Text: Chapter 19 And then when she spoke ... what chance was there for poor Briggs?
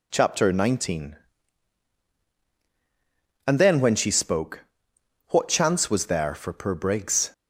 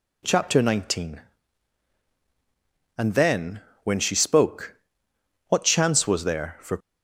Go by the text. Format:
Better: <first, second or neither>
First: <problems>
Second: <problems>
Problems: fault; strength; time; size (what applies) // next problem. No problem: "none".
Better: first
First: none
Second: pauses between "then" and "when"; slight; at 3.5 s; 0.24 s long // stops before "poor Briggs"; at 6.7 s